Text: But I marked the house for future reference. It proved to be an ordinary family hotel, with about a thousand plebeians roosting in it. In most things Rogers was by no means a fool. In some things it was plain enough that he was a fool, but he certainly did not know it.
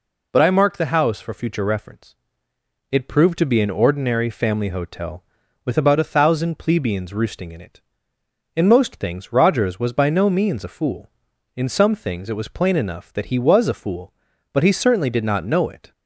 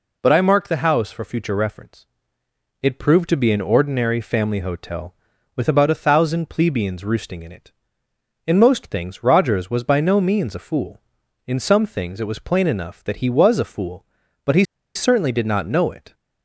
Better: first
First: none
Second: pauses between "he" and "certainly"; slight; at 14.6 s; 0.31 s long

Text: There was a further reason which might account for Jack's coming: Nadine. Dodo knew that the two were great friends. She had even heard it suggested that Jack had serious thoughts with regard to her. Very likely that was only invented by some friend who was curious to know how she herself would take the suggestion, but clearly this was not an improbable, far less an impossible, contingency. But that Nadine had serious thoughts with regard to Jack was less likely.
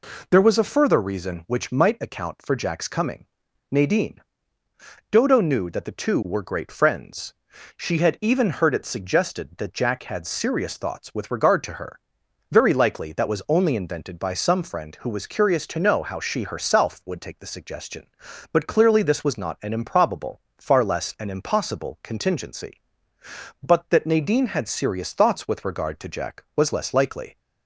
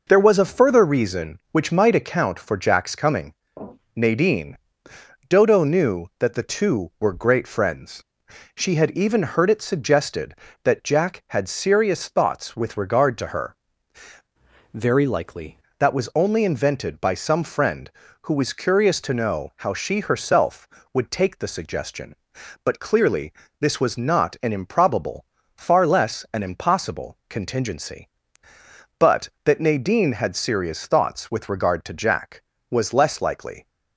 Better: first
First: none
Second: changes voice from "Very" to "likely"; from 14.7 to 15.5 s; 0.8 s long // pauses between "clearly" and "this"; slight; at 23.3 s; 0.28 s long

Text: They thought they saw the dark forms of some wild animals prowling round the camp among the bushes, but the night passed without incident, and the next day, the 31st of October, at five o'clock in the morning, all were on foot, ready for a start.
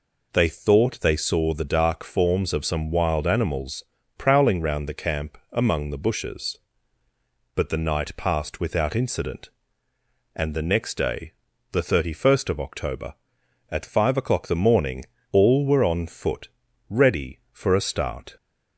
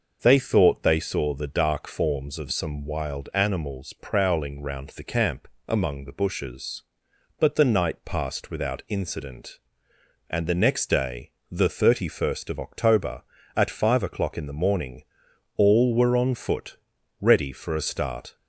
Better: second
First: pauses between "animals" and "prowling"; slight; at 3.8 s; 0.36 s long // pauses between "camp" and "among"; slight; at 5.3 s; 0.16 s long // skips "in"; at 14.4 s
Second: pauses between "camp" and "among"; slight; at 5.4 s; 0.20 s long

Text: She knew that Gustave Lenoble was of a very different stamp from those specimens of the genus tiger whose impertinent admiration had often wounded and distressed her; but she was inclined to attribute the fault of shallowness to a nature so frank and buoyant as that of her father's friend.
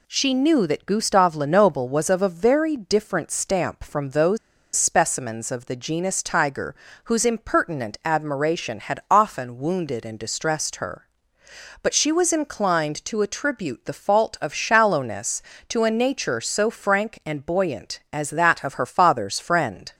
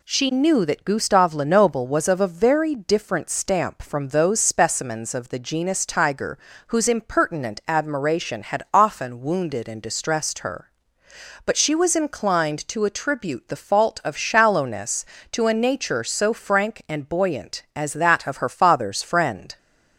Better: second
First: pauses between "those" and "specimens"; at 4.3 s; 0.38 s long // pauses between "tiger" and "whose"; slight; at 6.7 s; 0.30 s long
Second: pauses between "tiger" and "whose"; slight; at 6.3 s; 0.30 s long

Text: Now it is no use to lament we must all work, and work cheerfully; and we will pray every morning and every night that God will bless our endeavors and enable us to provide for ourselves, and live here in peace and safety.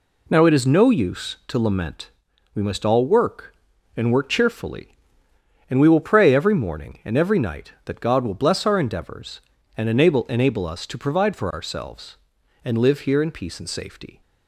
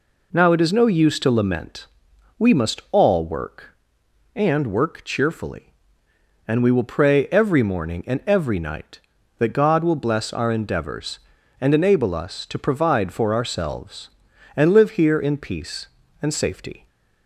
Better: second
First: pauses between "lament" and "we"; at 2.0 s; 0.44 s long // says "enable" twice; at 10.2 s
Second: pauses between "lament" and "we"; noticeable; at 1.8 s; 0.52 s long

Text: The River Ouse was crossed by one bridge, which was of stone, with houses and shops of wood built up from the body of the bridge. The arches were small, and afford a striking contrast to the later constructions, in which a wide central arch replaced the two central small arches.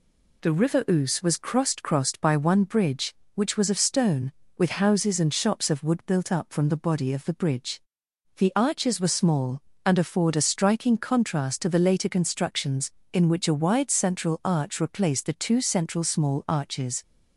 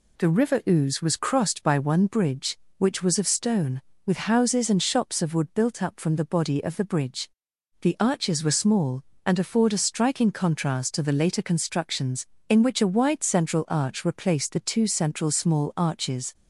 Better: second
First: says "crossed" twice; at 1.8 s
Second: none

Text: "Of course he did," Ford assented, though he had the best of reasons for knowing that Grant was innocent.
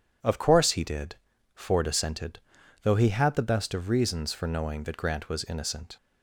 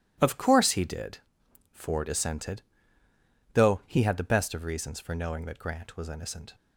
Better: neither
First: none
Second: none

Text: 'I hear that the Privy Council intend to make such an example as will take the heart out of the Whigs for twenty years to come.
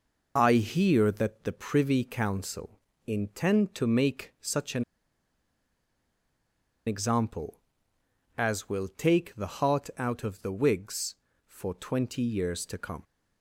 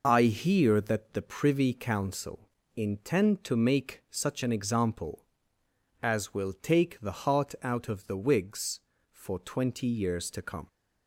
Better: second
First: pauses between "Council" and "intend"; slight; at 2.7 s; 0.28 s long // pauses between "an" and "example"; strong; at 4.8 s; 2.0 s long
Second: pauses between "Council" and "intend"; slight; at 2.4 s; 0.28 s long

